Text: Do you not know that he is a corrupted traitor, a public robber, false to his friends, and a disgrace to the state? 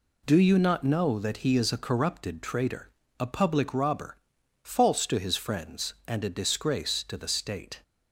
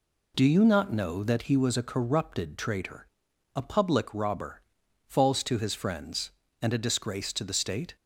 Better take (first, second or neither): first